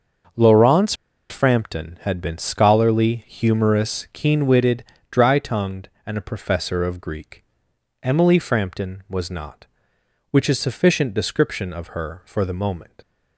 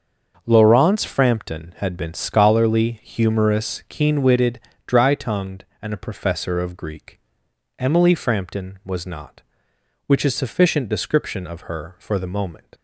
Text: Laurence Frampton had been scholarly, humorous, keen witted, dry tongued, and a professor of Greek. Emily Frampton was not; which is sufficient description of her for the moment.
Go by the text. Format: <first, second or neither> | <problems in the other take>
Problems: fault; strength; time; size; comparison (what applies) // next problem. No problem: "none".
second | starts louder than the rest; until 1.7 s; 6.5 dB; also in the second // pauses between "Laurence" and "Frampton"; at 0.9 s; 0.36 s long